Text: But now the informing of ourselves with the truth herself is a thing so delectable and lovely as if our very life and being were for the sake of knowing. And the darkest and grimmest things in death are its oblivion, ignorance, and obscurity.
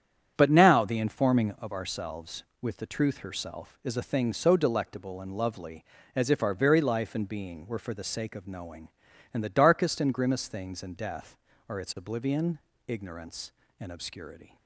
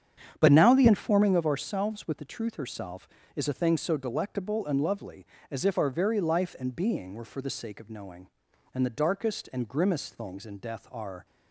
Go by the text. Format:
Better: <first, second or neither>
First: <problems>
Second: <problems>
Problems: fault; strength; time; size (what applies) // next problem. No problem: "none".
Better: first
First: starts louder than the rest; strong; until 1.3 s; 9 dB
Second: starts louder than the rest; strong; until 1.4 s; 8.5 dB // stops before "its oblivion ignorance and obscurity"; at 11.2 s